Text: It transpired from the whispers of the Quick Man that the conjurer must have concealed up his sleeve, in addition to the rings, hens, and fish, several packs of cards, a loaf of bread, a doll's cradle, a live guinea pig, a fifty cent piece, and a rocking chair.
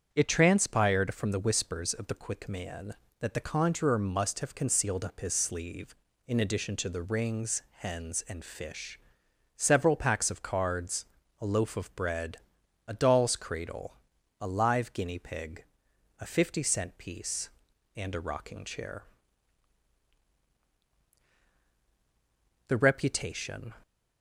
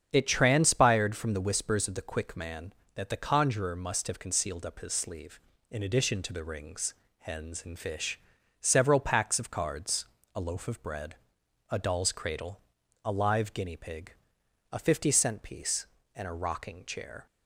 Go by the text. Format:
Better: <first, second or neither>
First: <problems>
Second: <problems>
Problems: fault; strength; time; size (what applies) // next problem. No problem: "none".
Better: second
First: starts louder than the rest; strong; until 1.1 s; 7.5 dB // goes on to say "The reputation"; noticeable; from 22.6 s on; 1.0 s long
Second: starts louder than the rest; strong; until 1.1 s; 7.5 dB